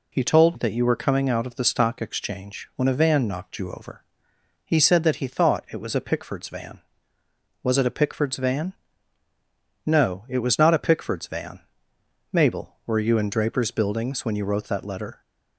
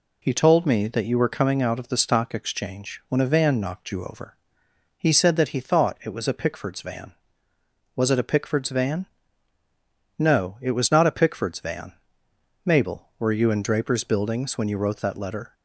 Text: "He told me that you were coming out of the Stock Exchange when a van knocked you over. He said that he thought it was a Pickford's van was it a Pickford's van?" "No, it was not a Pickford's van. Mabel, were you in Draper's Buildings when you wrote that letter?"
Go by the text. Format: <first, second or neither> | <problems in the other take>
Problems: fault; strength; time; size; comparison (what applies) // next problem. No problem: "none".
second | skips "me"; at 0.5 s